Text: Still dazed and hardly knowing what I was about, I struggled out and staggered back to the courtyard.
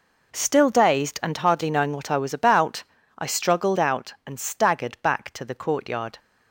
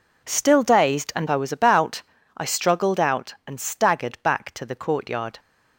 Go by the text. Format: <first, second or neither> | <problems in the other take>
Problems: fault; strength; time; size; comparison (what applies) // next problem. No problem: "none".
first | skips "hardly knowing what"; at 1.2 s